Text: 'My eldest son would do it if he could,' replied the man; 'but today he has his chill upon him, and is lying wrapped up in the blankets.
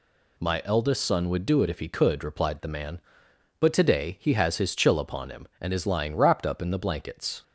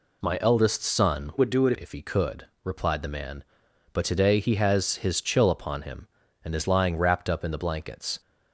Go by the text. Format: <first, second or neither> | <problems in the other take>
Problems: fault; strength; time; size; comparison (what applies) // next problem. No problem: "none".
first | changes voice from "would" to "it"; from 1.3 to 1.7 s; 0.4 s long